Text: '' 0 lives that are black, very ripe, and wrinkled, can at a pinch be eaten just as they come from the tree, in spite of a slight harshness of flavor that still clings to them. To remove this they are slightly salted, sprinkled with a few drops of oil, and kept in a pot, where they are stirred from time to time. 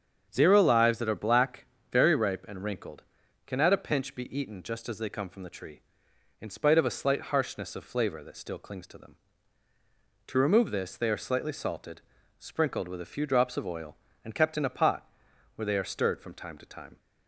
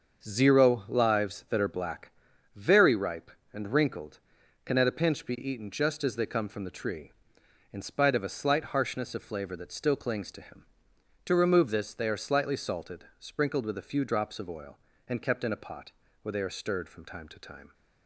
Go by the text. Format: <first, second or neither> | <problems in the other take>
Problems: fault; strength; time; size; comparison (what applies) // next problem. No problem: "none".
first | starts louder than the rest; until 1.2 s; 6.5 dB; strong in the first // says "him" for "them"; at 10.3 s